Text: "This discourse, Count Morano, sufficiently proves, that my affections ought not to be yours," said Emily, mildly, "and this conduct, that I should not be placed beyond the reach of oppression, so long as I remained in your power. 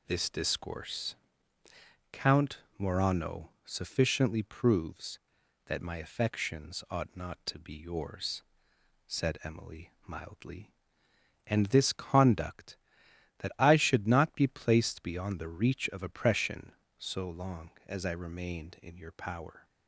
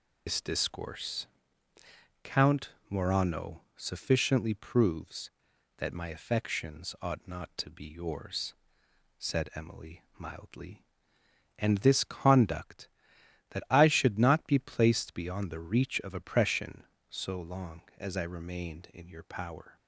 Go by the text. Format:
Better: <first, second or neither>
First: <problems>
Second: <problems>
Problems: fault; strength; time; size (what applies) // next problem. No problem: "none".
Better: first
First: pauses between "Count" and "Morano"; slight; at 2.5 s; 0.18 s long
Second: loses the start of "This"; at 0.2 s; 85 ms // pauses between "Count" and "Morano"; slight; at 2.7 s; 0.18 s long